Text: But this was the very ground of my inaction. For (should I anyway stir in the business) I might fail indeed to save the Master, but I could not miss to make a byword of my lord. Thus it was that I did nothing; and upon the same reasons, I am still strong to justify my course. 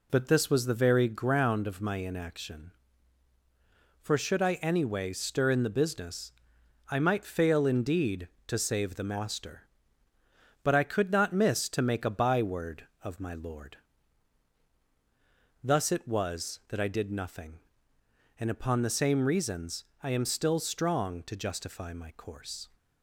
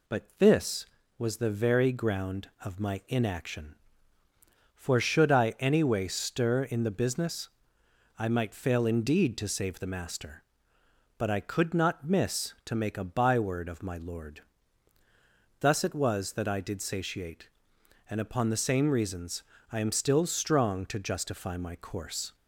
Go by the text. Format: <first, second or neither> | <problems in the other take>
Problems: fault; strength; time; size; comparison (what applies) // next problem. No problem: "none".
first | says "satiate" for "nothing"; at 16.8 s